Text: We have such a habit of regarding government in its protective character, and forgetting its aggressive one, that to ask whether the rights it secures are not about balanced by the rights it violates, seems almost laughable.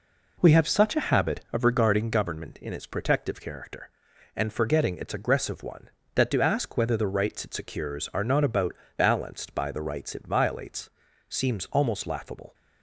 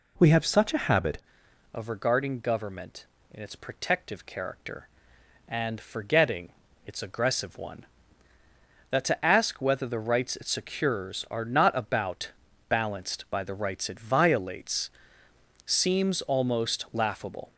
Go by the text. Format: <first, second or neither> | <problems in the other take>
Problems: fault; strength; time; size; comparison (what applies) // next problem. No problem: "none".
first | changes voice at "of"; from 1.7 s on; 15.8 s long // pauses between "forgetting" and "its"; at 6.4 s; 0.38 s long // pauses between "about" and "balanced"; at 12.3 s; 0.38 s long; slight in the first